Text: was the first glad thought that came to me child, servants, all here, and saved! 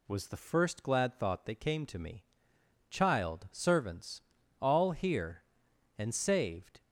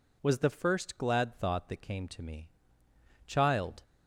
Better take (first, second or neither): first